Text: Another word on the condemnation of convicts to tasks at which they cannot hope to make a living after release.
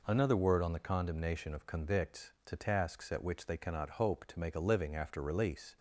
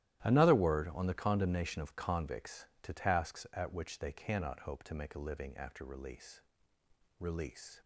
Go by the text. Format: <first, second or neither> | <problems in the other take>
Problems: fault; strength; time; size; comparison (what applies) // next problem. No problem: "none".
first | starts louder than the rest; strong; until 1.2 s; 13 dB // says "release" twice; at 7.1 s